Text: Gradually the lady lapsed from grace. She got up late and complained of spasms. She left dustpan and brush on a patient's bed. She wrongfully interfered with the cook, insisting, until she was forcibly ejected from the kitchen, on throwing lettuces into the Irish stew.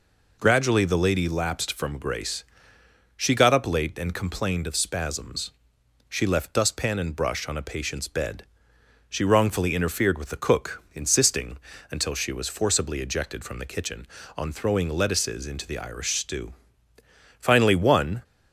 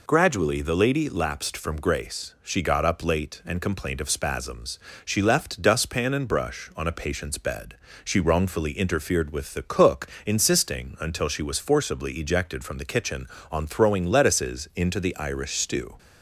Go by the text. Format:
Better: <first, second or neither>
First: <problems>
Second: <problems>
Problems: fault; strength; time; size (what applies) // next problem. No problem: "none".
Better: second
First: goes on to say "Finally one"; noticeable; from 17.3 s on; 0.84 s long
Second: none